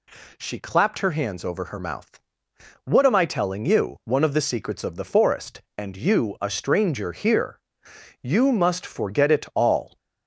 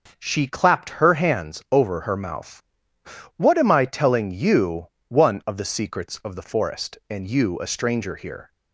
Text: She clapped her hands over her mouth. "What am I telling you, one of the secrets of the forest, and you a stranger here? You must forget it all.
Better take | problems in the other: first | starts louder than the rest; until 1.2 s; 6 dB // stops before "You must forget it all"; at 8.5 s

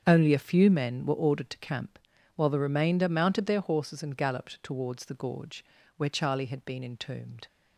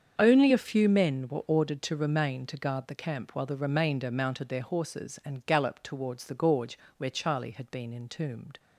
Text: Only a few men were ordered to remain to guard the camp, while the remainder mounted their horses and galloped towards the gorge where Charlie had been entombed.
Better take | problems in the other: second | starts louder than the rest; strong; until 1.0 s; 7 dB; strong in the second // skips "remain to guard the"; at 1.5 s // pauses between "gorge" and "where"; slight; at 5.6 s; 0.32 s long; slight in the second

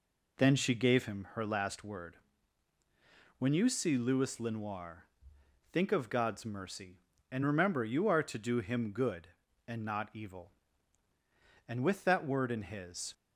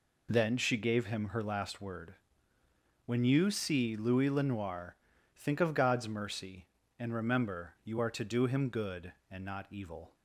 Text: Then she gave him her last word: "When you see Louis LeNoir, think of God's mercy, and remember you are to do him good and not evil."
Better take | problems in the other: second | goes on to say "And with that word in his"; from 11.6 s on; 1.4 s long

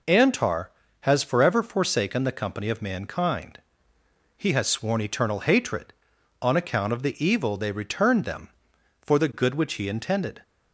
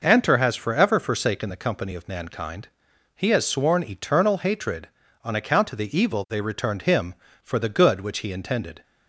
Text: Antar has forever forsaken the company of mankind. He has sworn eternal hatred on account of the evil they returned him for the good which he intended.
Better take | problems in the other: second | says "them" for "him"; at 8.2 s

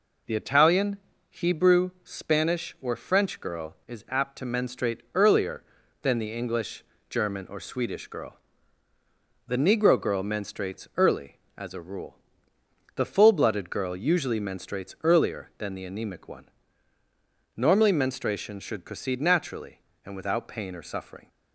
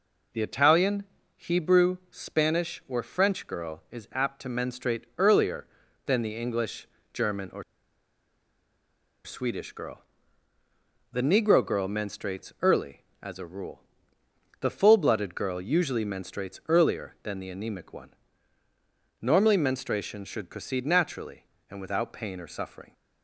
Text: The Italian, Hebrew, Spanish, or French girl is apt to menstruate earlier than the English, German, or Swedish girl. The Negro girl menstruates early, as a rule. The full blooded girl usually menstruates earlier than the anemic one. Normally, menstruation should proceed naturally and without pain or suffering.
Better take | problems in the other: first | pauses between "or" and "Swedish"; strong; at 7.6 s; 1.6 s long

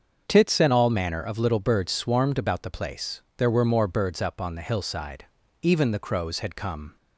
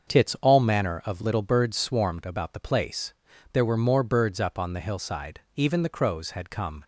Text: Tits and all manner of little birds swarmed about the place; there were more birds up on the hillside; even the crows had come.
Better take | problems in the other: first | starts louder than the rest; until 1.1 s; 6.5 dB; also in the first // skips "and"; at 0.3 s

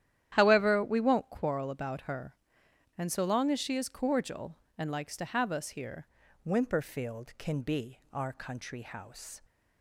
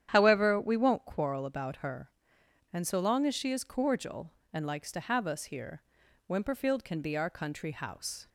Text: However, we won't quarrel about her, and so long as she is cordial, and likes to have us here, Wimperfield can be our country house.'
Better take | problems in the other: second | starts louder than the rest; strong; until 1.3 s; 11 dB; strong in the second // changes voice at "Wimperfield"; from 6.4 s on; 3.0 s long

